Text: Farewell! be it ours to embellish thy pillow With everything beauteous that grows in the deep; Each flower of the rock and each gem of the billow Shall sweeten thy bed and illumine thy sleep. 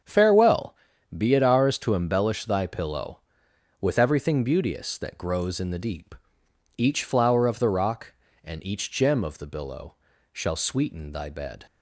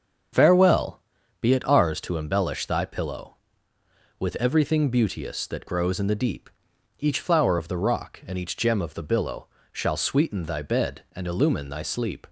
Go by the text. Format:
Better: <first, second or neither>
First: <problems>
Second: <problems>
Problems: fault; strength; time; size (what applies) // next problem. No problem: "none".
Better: second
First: starts louder than the rest; strong; until 1.4 s; 8 dB // pauses between "billow" and "Shall"; slight; at 9.9 s; 0.36 s long // stops before "and illumine thy sleep"; at 11.6 s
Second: starts louder than the rest; strong; until 1.7 s; 7 dB // pauses between "billow" and "Shall"; slight; at 9.4 s; 0.26 s long